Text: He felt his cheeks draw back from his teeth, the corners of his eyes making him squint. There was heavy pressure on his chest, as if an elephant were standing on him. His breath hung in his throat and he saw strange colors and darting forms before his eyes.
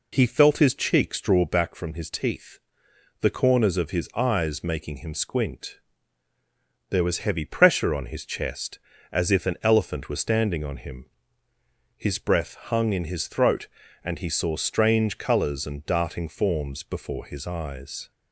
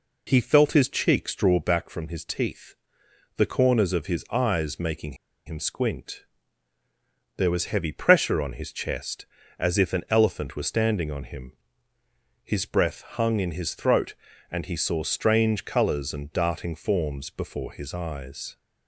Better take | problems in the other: first | pauses between "making" and "him"; slight; at 5.1 s; 0.32 s long

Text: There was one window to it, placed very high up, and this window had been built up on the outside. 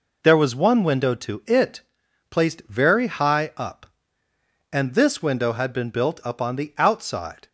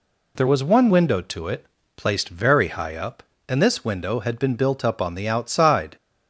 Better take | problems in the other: neither | none

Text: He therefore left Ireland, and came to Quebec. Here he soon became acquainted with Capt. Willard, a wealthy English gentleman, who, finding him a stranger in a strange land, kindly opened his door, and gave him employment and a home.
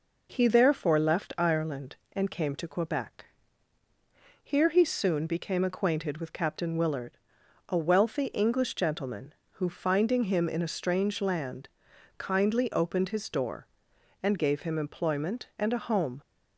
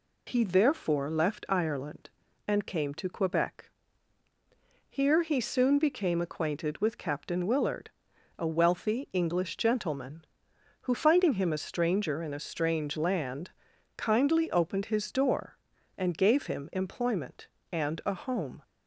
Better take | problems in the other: second | skips "a stranger"; at 10.4 s

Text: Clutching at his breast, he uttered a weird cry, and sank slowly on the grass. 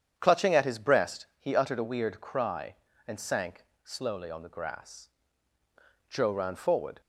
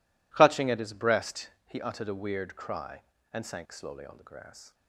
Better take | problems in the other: second | starts louder than the rest; strong; until 1.1 s; 8.5 dB // pauses between "sank" and "slowly"; slight; at 3.6 s; 0.18 s long // goes on to say "Joe ran forward"; noticeable; from 6.0 s on; 0.92 s long

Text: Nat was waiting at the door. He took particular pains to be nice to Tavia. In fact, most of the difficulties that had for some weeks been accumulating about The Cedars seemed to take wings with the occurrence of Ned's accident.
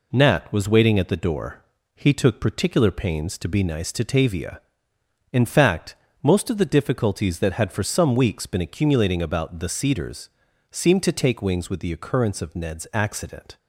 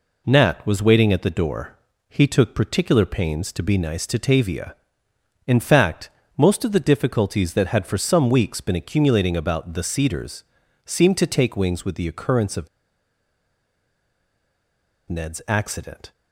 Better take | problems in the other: first | pauses between "Cedars" and "seemed"; at 10.4 s; 0.42 s long; also in the first // pauses between "of" and "Ned's"; strong; at 12.6 s; 2.4 s long

